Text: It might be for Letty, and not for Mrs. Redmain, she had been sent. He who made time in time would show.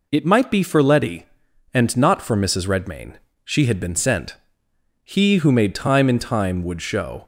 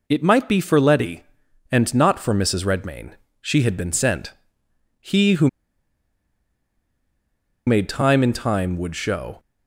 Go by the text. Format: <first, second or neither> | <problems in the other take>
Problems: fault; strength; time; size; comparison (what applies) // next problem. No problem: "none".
first | pauses between "who" and "made"; strong; at 5.4 s; 2.1 s long